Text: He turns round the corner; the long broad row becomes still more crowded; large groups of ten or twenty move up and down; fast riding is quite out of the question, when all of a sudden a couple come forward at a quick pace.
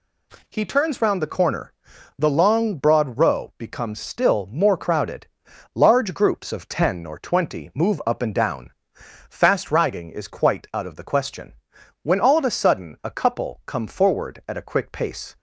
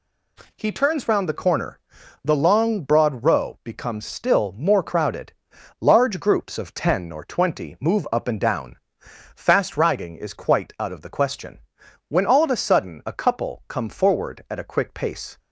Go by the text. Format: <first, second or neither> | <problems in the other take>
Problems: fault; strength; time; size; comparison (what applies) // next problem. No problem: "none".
neither | none